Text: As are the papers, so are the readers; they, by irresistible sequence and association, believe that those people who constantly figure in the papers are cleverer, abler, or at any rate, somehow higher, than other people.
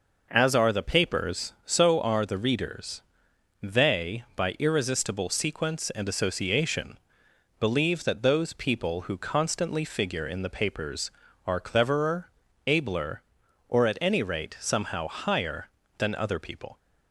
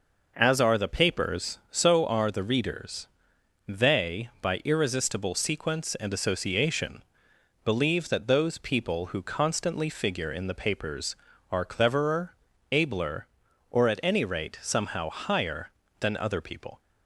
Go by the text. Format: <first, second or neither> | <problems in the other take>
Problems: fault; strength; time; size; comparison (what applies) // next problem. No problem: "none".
neither | none